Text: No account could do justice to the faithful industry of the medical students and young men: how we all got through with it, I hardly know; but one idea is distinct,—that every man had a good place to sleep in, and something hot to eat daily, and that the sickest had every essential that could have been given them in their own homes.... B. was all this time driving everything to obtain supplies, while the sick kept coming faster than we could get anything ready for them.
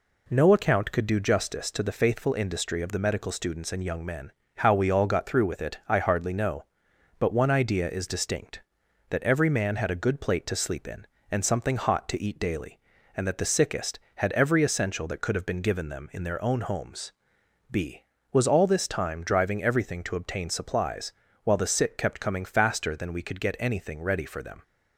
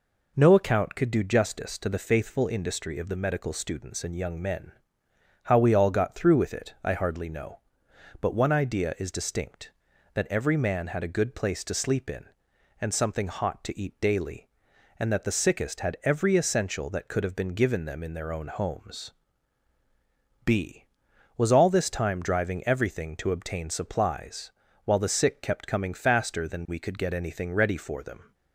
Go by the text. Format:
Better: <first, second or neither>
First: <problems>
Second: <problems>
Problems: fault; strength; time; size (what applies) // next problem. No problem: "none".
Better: second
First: says "plate" for "place"; at 10.1 s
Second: none